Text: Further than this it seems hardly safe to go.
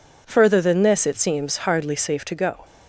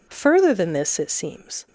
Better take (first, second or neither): first